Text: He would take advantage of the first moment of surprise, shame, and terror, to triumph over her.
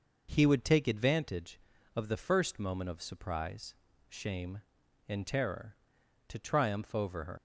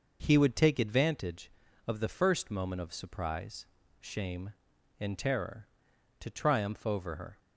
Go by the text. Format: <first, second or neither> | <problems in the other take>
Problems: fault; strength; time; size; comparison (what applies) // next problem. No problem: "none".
second | leaves "her" unfinished; at 7.3 s; 100 ms